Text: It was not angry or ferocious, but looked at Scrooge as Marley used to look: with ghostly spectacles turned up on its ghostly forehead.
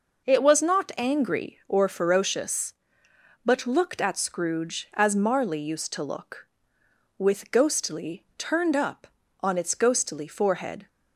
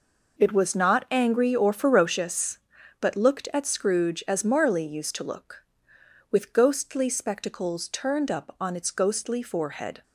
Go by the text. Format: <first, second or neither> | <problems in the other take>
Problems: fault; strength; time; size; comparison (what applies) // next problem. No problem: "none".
second | skips "spectacles"; at 8.3 s